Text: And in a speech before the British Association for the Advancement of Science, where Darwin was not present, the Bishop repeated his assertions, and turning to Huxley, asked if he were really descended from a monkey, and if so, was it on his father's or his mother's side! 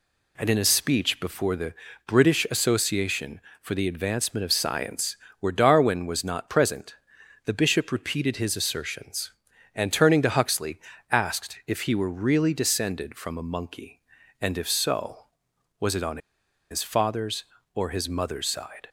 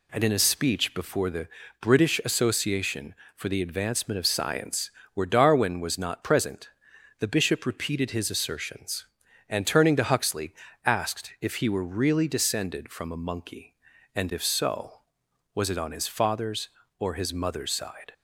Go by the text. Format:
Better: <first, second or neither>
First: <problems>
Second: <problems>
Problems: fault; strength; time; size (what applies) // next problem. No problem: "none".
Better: second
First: pauses between "the" and "British"; slight; at 1.7 s; 0.34 s long // pauses between "on" and "his"; noticeable; at 16.1 s; 0.52 s long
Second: pauses between "the" and "British"; slight; at 1.4 s; 0.34 s long